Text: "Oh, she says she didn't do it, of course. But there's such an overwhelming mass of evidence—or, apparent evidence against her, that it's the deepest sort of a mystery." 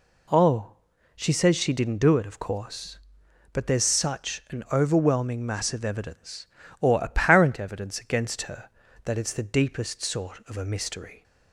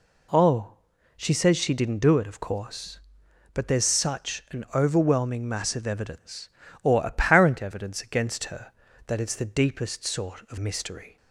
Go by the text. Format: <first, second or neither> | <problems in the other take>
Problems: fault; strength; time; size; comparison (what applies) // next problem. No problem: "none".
first | skips "a"; at 10.5 s